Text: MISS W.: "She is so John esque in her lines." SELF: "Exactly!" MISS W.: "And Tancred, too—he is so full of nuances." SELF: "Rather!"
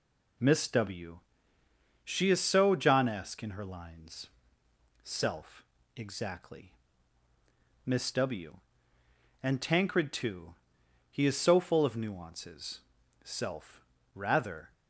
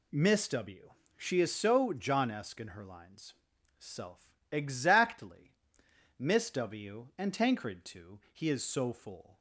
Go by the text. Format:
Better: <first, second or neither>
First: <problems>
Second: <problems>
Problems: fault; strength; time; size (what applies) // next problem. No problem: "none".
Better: first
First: none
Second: stops before "of nuances SELF Rather"; at 9.3 s